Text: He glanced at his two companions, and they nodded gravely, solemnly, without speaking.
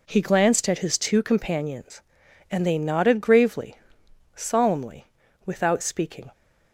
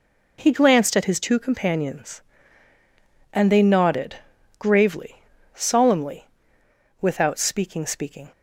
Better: first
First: none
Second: pauses between "nodded" and "gravely"; at 4.1 s; 0.42 s long // says "speaking" twice; at 7.8 s

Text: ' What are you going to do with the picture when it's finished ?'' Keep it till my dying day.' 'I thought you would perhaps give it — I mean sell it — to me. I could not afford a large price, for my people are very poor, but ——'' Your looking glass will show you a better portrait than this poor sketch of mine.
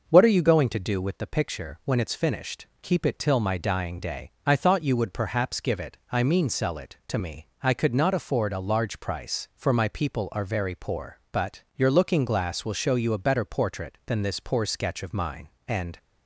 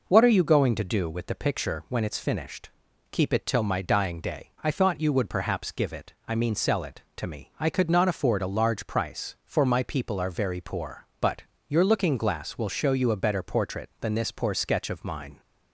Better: second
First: goes on to say "And"; slight; from 15.6 s on; 0.30 s long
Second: none

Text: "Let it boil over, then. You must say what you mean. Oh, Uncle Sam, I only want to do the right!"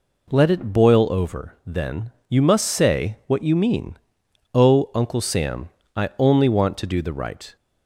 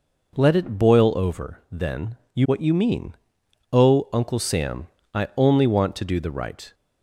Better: first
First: none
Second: skips "must say"; at 2.4 s

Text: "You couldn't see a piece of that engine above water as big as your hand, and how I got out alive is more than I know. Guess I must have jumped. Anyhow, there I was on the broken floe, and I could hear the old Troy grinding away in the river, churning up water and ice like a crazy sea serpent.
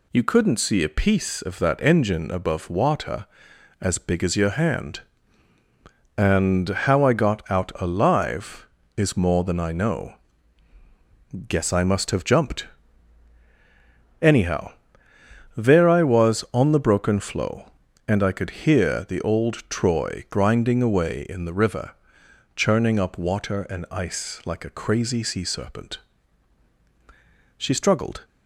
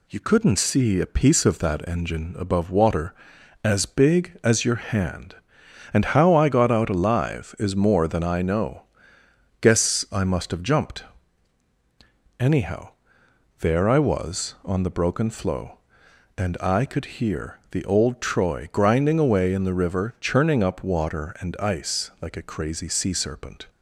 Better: second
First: goes on to say "She struggled"; noticeable; from 27.5 s on; 0.66 s long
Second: none

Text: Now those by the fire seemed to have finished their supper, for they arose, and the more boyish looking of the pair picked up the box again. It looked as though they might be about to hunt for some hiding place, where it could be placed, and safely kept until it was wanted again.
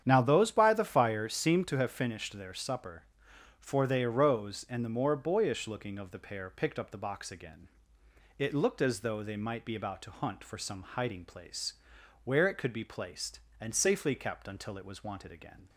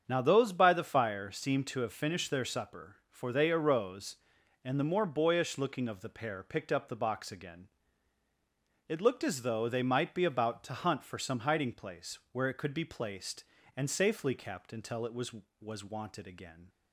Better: first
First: starts louder than the rest; strong; until 1.0 s; 9 dB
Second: starts louder than the rest; strong; until 1.0 s; 7.5 dB // says "was" twice; at 15.5 s

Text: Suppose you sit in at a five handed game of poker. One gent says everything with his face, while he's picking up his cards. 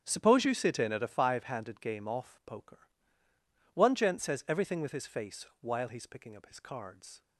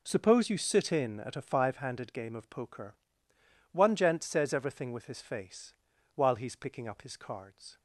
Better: second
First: starts louder than the rest; strong; until 1.0 s; 8.5 dB // says "off" for "of"; at 2.0 s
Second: none

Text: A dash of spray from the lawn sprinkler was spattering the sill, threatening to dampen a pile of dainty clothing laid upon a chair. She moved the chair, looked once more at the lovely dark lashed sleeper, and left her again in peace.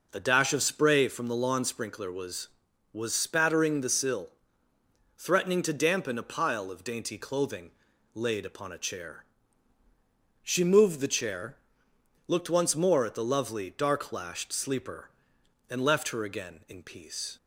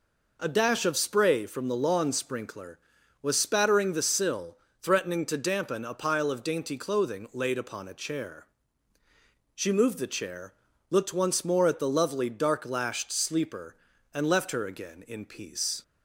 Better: second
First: says "was" twice; at 2.9 s // pauses between "clothing" and "laid"; noticeable; at 7.6 s; 0.46 s long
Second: none

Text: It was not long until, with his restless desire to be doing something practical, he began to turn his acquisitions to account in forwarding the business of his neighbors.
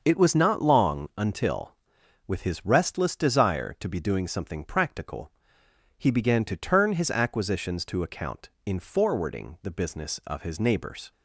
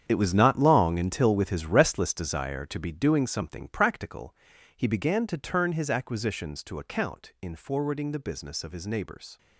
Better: first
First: starts louder than the rest; until 1.0 s; 6.5 dB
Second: gets quieter; strong; throughout; 12.5 dB // starts louder than the rest; strong; until 1.0 s; 8.5 dB

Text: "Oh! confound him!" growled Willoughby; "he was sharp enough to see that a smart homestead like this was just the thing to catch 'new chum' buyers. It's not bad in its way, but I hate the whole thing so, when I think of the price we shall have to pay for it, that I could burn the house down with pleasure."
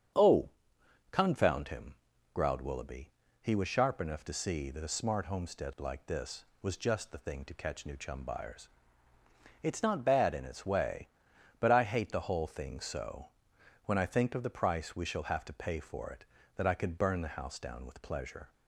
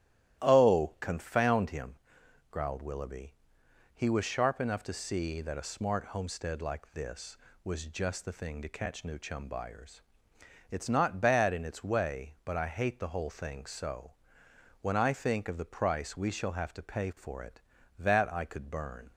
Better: first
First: starts louder than the rest; strong; until 1.7 s; 8 dB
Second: starts louder than the rest; strong; until 1.4 s; 13 dB // stops before "the house down with pleasure"; at 19.1 s

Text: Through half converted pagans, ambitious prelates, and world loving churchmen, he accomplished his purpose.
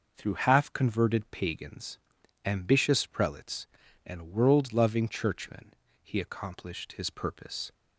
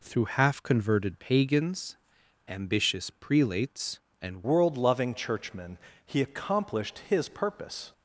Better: first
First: none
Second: changes voice at "world"; from 4.4 s on; 3.5 s long

